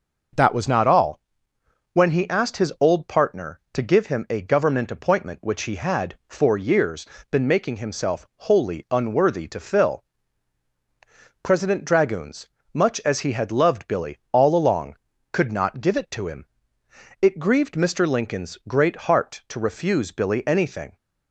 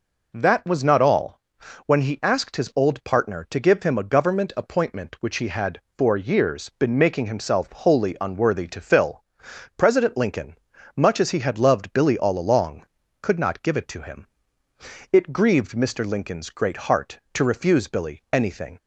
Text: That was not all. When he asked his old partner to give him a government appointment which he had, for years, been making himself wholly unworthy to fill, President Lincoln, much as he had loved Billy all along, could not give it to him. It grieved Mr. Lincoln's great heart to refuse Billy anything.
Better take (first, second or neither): second